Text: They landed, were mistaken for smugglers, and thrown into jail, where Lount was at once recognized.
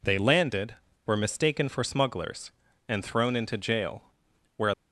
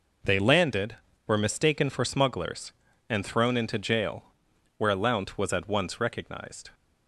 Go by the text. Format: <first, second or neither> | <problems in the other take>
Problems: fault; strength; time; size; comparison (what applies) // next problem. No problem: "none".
second | stops before "Lount was at once recognized"; at 4.7 s